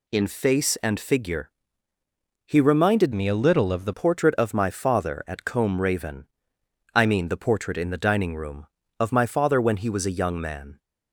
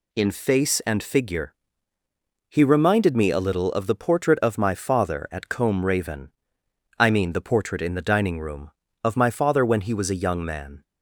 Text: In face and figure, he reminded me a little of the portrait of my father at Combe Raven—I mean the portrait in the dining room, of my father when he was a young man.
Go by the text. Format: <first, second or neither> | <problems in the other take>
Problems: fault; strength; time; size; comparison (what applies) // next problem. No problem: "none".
second | changes voice from "me" to "the"; from 3.1 to 3.9 s; 0.8 s long